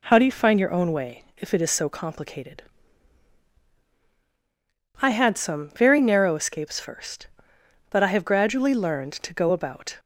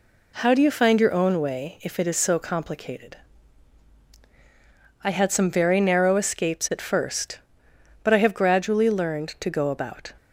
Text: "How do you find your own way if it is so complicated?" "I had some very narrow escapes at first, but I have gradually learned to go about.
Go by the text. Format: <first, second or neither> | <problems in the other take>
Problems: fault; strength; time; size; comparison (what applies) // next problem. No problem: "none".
second | skips "at"; at 6.8 s